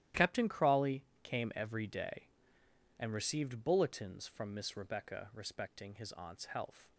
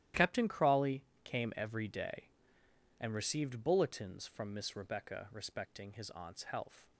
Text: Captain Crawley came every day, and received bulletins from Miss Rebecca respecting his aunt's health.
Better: neither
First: starts louder than the rest; strong; until 1.3 s; 13 dB // pauses between "Crawley" and "came"; slight; at 1.0 s; 0.20 s long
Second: starts louder than the rest; strong; until 1.3 s; 13 dB // pauses between "Crawley" and "came"; slight; at 1.0 s; 0.22 s long

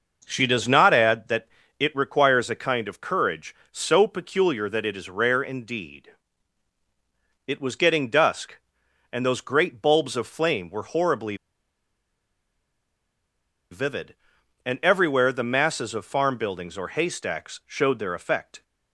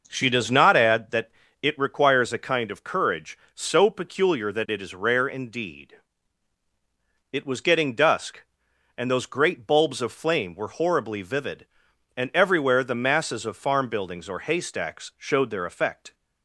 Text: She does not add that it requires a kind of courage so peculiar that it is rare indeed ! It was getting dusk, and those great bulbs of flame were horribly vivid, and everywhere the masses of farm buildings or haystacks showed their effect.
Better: second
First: pauses between "that" and "it"; slight; at 1.4 s; 0.32 s long // pauses between "horribly" and "vivid"; strong; at 11.3 s; 2.3 s long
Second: pauses between "that" and "it"; slight; at 1.2 s; 0.32 s long

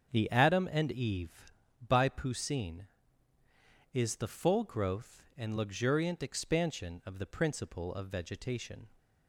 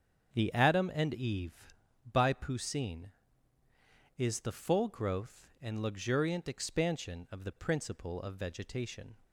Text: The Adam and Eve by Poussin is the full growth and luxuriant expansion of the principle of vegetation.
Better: neither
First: starts louder than the rest; strong; until 1.1 s; 7.5 dB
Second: starts louder than the rest; strong; until 1.3 s; 7.5 dB

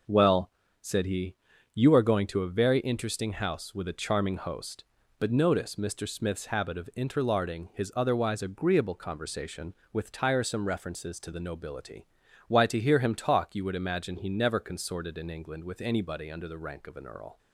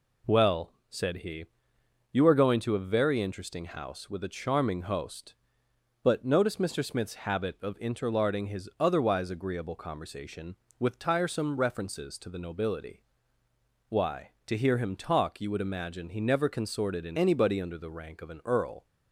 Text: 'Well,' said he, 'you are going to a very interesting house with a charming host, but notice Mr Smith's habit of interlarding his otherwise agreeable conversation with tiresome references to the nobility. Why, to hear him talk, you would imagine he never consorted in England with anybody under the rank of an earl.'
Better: first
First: none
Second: skips "England with"; at 17.1 s

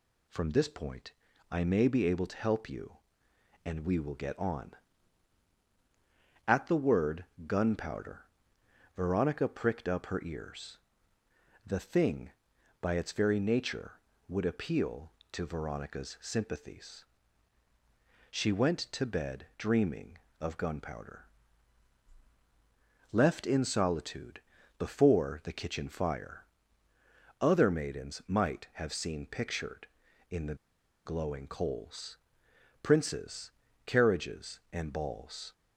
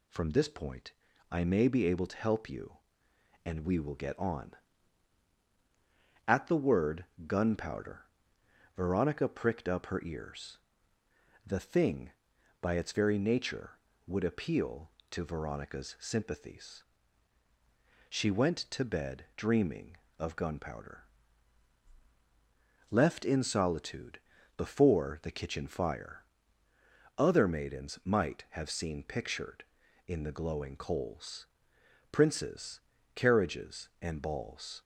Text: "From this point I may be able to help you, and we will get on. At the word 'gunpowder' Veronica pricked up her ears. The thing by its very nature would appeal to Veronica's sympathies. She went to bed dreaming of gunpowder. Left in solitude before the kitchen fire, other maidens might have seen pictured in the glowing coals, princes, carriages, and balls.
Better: second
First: pauses between "point" and "I"; at 1.1 s; 0.38 s long // pauses between "word" and "gunpowder"; slight; at 7.2 s; 0.20 s long // pauses between "gunpowder" and "Veronica"; noticeable; at 8.2 s; 0.70 s long // pauses between "solitude" and "before"; slight; at 24.4 s; 0.36 s long // pauses between "the" and "glowing"; noticeable; at 30.5 s; 0.50 s long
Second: pauses between "point" and "I"; at 0.9 s; 0.38 s long // pauses between "word" and "gunpowder"; slight; at 7.0 s; 0.20 s long // pauses between "gunpowder" and "Veronica"; noticeable; at 8.0 s; 0.70 s long // pauses between "solitude" and "before"; slight; at 24.1 s; 0.36 s long

